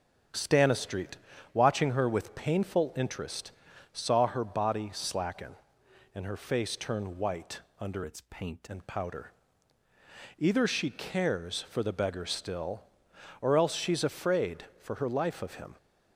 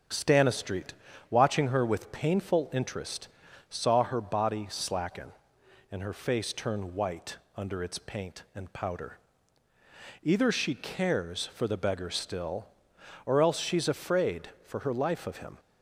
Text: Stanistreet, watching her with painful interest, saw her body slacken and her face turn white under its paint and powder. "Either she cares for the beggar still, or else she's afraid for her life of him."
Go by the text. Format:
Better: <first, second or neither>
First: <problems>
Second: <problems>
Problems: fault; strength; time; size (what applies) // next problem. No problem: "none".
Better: second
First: starts louder than the rest; strong; until 1.6 s; 7 dB // pauses between "white" and "under"; slight; at 7.6 s; 0.18 s long // changes voice from "its" to "paint"; from 8.0 to 8.6 s; 0.6 s long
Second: starts louder than the rest; until 1.4 s; 6.5 dB // pauses between "white" and "under"; slight; at 7.3 s; 0.18 s long